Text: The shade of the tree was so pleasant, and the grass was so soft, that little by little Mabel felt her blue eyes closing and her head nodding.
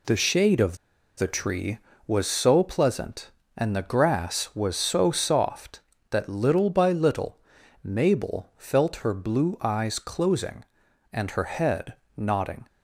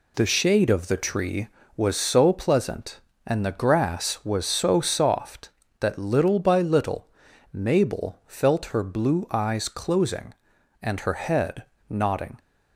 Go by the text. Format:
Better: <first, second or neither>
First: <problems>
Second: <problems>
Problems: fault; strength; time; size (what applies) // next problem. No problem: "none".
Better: second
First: pauses between "of" and "the"; at 0.7 s; 0.40 s long // pauses between "little" and "Mabel"; noticeable; at 7.3 s; 0.46 s long // pauses between "head" and "nodding"; slight; at 11.9 s; 0.22 s long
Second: pauses between "little" and "Mabel"; noticeable; at 7.0 s; 0.46 s long // pauses between "head" and "nodding"; slight; at 11.6 s; 0.25 s long